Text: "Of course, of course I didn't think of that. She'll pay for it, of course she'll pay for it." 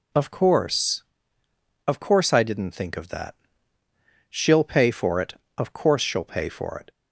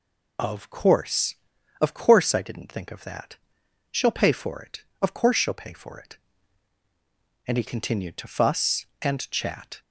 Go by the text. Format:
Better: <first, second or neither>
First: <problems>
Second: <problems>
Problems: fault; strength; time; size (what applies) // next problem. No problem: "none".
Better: first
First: none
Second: goes on to say "And he continued to fuss and chat"; strong; from 7.4 s on; 2.3 s long